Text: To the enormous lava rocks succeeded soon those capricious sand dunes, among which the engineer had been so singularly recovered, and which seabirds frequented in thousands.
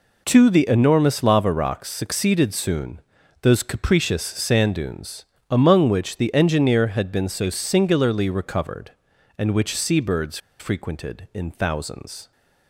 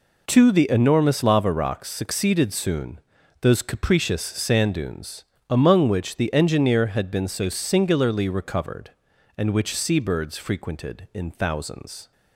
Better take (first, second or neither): second